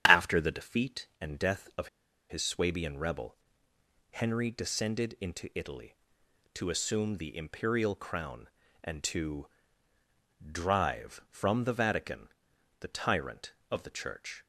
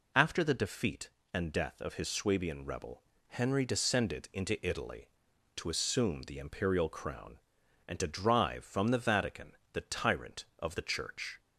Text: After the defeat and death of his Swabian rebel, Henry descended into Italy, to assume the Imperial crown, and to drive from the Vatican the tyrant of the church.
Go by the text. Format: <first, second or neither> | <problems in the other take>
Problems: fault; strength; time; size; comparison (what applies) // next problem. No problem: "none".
second | starts louder than the rest; strong; until 1.0 s; 9 dB // pauses between "of" and "his"; at 1.8 s; 0.41 s long // pauses between "to" and "drive"; at 9.4 s; 1.0 s long // pauses between "Vatican" and "the"; noticeable; at 12.2 s; 0.50 s long; slight in the second